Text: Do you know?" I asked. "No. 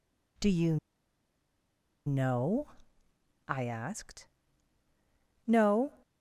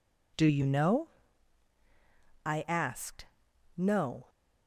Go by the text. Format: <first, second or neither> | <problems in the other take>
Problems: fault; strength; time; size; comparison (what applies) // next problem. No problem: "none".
second | pauses between "you" and "know"; strong; at 0.7 s; 1.3 s long